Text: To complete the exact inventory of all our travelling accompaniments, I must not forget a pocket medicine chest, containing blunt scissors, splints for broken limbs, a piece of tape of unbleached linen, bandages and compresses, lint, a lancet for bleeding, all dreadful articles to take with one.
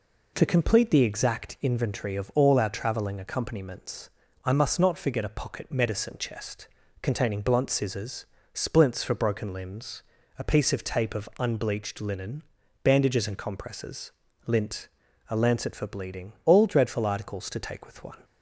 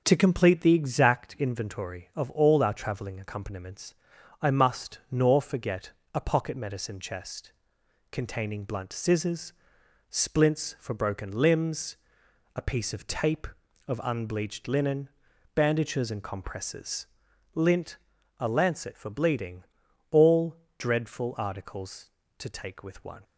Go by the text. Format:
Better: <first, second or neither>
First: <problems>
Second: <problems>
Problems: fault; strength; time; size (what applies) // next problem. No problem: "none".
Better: first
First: none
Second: starts louder than the rest; noticeable; until 1.0 s; 6 dB // says "nor" for "not"; at 5.0 s // pauses between "forget" and "a"; slight; at 5.9 s; 0.22 s long // pauses between "all" and "dreadful"; slight; at 20.5 s; 0.20 s long